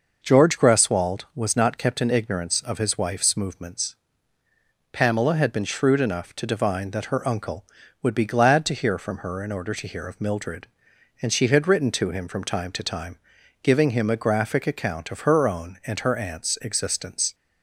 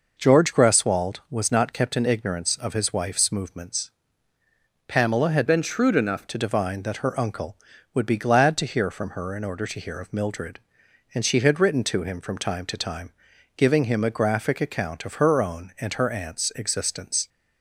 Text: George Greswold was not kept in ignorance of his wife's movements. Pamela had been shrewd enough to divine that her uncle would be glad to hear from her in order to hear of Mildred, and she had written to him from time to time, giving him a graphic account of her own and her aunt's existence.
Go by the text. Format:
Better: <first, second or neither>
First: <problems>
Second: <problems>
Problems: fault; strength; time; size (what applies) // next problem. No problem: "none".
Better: first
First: none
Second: changes voice from "been" to "enough"; from 5.4 to 6.2 s; 0.8 s long